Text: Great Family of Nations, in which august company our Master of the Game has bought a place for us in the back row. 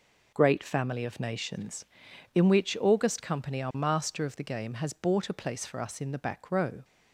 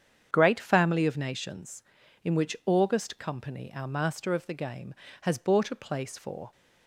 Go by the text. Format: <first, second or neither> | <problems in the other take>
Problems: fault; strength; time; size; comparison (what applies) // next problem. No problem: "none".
first | starts louder than the rest; strong; until 1.3 s; 8 dB // stops before "us in the back row"; at 6.5 s